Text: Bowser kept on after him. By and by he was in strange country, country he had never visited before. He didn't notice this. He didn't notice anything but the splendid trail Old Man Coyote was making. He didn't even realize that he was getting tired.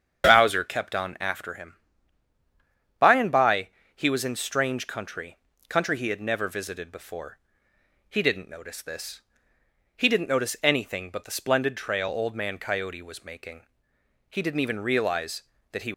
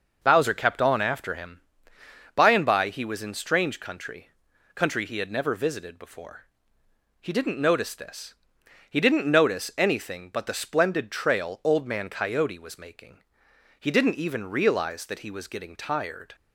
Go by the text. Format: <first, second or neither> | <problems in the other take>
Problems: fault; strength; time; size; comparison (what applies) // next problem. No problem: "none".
second | starts louder than the rest; strong; until 1.3 s; 8 dB // pauses between "by" and "he"; slight; at 3.6 s; 0.26 s long // stops before "was getting tired"; at 15.9 s